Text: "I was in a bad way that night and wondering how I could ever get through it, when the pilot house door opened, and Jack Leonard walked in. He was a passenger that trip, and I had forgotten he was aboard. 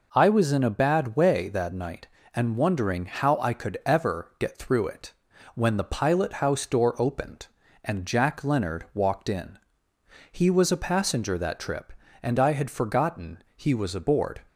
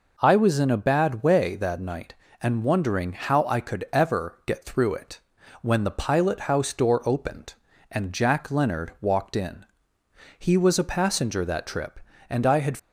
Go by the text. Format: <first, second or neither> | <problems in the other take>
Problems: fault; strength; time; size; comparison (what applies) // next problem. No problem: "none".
first | stops before "forgotten he was aboard"; at 12.7 s